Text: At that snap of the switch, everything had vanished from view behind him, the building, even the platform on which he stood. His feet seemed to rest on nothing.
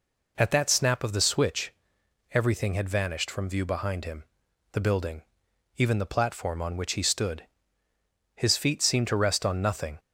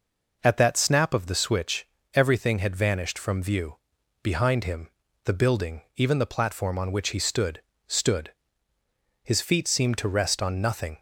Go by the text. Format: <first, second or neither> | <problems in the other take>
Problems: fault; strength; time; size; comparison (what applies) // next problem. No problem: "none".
first | pauses between "view" and "behind"; noticeable; at 3.7 s; 0.48 s long // says "stood" twice; at 7.8 s